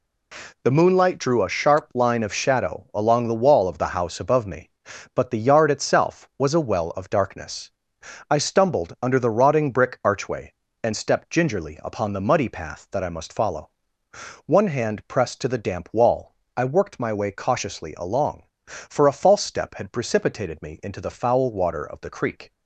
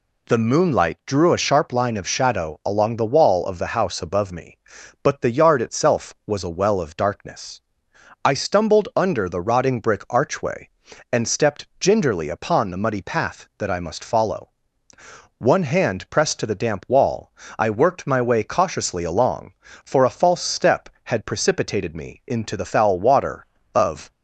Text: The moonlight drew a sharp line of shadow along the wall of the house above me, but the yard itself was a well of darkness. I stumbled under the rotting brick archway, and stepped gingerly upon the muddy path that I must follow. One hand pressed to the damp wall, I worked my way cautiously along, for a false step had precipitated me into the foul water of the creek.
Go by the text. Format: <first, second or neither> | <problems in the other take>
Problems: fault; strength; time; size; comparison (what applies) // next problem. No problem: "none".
first | stops before "the creek"; at 24.1 s